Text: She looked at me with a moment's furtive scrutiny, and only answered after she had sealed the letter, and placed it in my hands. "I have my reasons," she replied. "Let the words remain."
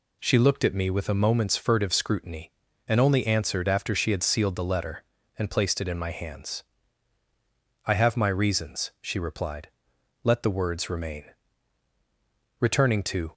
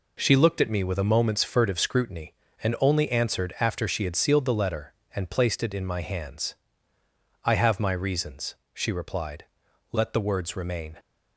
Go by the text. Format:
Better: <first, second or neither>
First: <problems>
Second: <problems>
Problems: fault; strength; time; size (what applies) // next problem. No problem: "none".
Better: second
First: goes on to say "Returning to"; noticeable; from 12.5 s on; 0.72 s long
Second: none